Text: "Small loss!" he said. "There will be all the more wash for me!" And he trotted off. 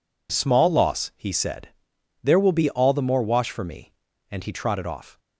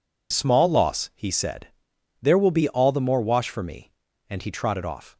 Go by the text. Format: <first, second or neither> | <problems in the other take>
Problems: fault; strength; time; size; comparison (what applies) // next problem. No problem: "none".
first | loses the start of "Small"; at 0.3 s; 20 ms